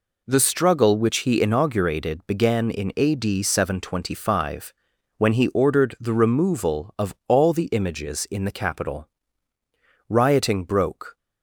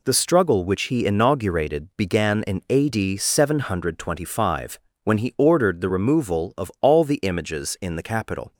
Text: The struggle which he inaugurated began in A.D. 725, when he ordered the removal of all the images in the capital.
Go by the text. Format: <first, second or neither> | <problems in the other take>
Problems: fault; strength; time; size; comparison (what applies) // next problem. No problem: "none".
second | goes on to say "Rioting broke"; noticeable; from 10.0 s on; 1.0 s long